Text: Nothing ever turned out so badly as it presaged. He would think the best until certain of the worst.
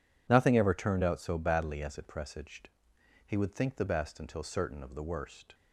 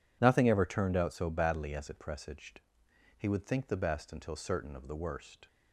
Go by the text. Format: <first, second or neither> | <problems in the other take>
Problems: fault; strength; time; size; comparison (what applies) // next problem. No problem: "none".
neither | none